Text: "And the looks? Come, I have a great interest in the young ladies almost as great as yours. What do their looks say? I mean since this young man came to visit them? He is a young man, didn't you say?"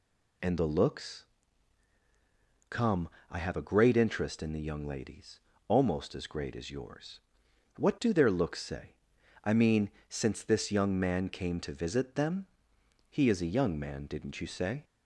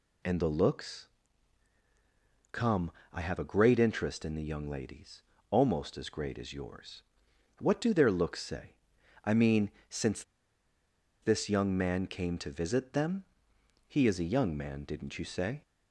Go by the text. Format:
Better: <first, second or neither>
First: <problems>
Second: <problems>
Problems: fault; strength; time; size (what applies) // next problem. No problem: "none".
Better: first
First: pauses between "ladies" and "almost"; slight; at 5.3 s; 0.28 s long // pauses between "mean" and "since"; slight; at 9.8 s; 0.20 s long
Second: pauses between "ladies" and "almost"; slight; at 5.2 s; 0.28 s long // pauses between "mean" and "since"; slight; at 9.7 s; 0.20 s long // pauses between "since" and "this"; at 10.2 s; 0.99 s long